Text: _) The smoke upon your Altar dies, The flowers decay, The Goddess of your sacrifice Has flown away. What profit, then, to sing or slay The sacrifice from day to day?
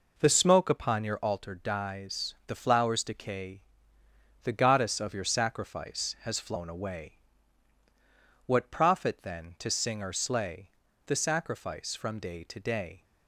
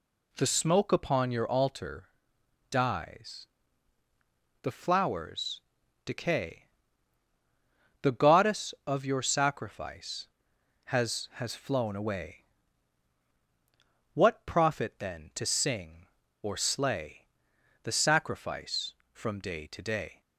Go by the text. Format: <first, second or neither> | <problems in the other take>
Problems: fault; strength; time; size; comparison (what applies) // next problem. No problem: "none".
first | pauses between "Altar" and "dies"; noticeable; at 2.0 s; 0.62 s long // pauses between "flowers" and "decay"; noticeable; at 5.6 s; 0.46 s long // says "Has" twice; at 11.3 s // pauses between "slay" and "The"; noticeable; at 17.2 s; 0.56 s long; slight in the first